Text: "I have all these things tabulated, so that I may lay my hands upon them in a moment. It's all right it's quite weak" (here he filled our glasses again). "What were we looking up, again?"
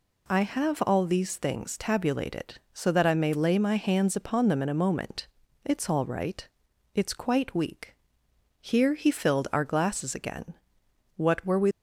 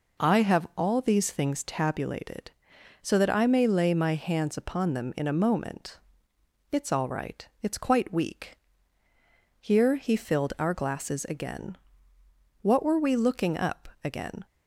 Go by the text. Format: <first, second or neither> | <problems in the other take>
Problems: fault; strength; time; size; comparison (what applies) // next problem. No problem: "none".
second | pauses between "right" and "it's"; noticeable; at 6.4 s; 0.50 s long; slight in the second // stops before "looking up again"; at 11.7 s